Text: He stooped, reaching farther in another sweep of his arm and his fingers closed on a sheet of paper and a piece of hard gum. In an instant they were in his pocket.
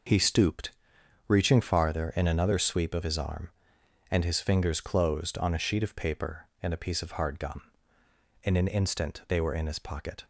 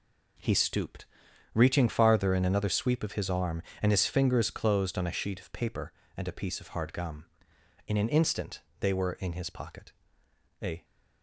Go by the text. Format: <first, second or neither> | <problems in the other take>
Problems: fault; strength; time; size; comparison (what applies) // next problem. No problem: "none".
first | pauses between "instant" and "they"; slight; at 8.6 s; 0.18 s long // goes on to say "A"; slight; from 10.6 s on; 0.24 s long